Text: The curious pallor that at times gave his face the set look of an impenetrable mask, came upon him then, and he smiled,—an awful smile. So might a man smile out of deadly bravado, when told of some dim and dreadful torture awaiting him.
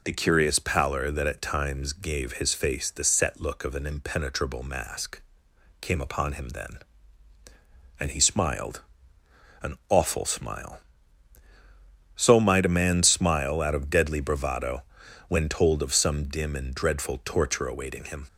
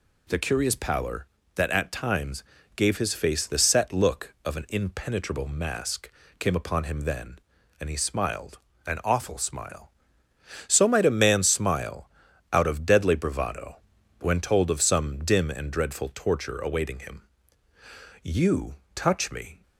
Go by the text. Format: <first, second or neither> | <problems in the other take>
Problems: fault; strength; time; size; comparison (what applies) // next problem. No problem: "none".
first | pauses between "times" and "gave"; slight; at 2.4 s; 0.32 s long // pauses between "smile" and "out"; at 12.0 s; 0.44 s long // goes on to say "You touch me"; from 18.2 s on; 1.4 s long